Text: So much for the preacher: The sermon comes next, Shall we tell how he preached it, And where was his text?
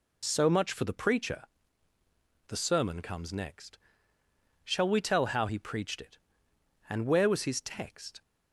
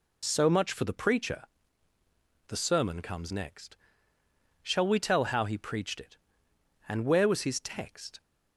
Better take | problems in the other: neither | none

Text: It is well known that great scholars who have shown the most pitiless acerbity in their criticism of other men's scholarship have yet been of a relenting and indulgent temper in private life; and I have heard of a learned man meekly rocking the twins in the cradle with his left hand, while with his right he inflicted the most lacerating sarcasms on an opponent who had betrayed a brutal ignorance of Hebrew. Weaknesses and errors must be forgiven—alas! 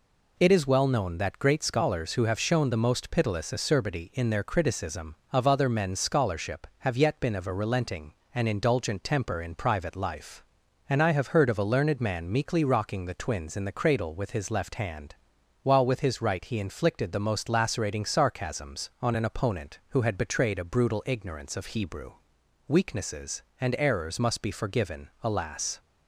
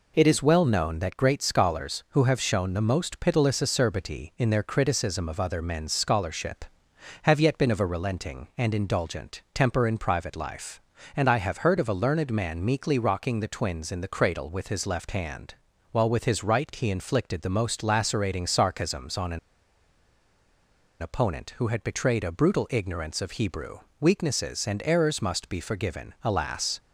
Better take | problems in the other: first | pauses between "an" and "opponent"; strong; at 19.3 s; 1.6 s long

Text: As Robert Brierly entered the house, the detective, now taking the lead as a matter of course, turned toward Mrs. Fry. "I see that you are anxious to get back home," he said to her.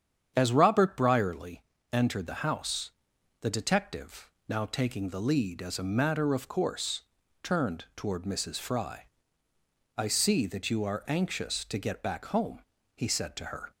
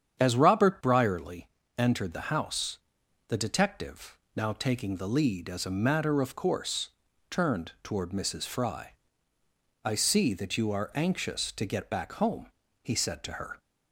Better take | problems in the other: neither | starts louder than the rest; strong; the same in both // pauses between "Brierly" and "entered"; slight; the same in both

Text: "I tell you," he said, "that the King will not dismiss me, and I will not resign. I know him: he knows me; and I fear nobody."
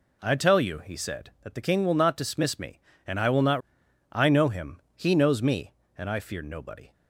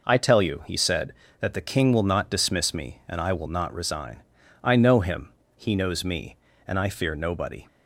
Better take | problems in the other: second | skips "resign"; at 3.8 s

